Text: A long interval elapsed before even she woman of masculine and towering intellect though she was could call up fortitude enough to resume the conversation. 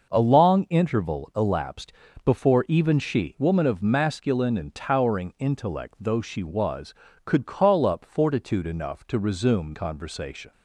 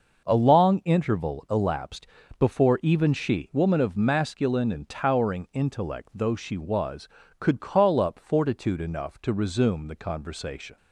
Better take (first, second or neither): second